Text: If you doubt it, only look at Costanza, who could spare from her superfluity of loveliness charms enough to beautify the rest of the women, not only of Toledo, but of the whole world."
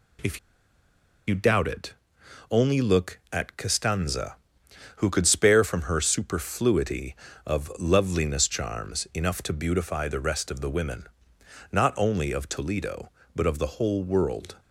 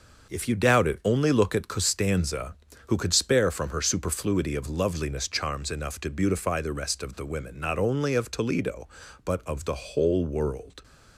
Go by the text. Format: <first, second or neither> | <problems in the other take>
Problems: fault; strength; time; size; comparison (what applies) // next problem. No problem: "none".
second | pauses between "If" and "you"; noticeable; at 0.3 s; 0.89 s long